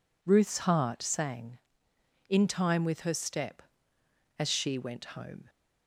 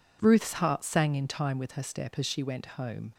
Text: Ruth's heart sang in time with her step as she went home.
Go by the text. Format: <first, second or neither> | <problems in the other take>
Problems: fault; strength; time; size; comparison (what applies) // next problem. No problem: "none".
neither | none